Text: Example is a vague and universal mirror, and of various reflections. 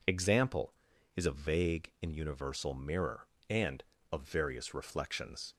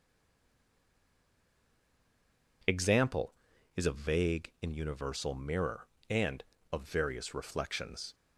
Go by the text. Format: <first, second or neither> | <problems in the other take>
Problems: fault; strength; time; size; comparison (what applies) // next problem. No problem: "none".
first | stays silent before the first word; strong; until 2.6 s; 2.6 s long